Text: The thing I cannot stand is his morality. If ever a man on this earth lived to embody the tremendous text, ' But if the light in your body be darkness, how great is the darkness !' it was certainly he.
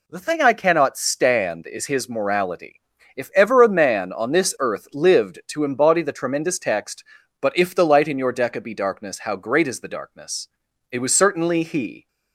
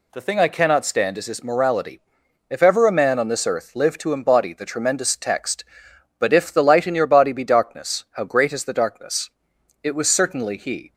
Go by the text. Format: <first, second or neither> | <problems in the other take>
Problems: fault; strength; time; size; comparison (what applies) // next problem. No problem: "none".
second | says "deca" for "body"; at 8.3 s